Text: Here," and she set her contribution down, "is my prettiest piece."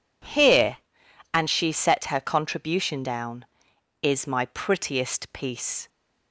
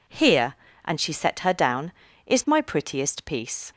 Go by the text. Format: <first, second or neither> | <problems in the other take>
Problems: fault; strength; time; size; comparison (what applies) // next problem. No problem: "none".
first | skips "contribution"; at 1.5 s